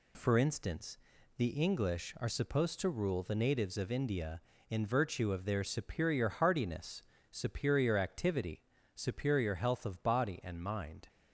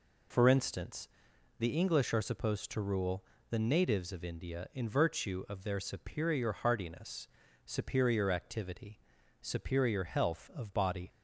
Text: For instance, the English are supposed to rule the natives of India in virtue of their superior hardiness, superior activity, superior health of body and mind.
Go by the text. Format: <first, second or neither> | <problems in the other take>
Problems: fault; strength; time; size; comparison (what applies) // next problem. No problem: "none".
first | pauses between "rule" and "the"; slight; at 3.2 s; 0.28 s long // stops before "and mind"; at 11.0 s